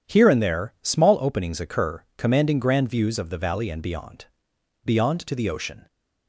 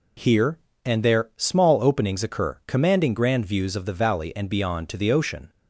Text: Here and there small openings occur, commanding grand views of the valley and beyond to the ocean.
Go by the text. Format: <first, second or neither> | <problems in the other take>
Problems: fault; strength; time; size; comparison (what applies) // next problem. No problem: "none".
second | says "beyond" twice; at 4.8 s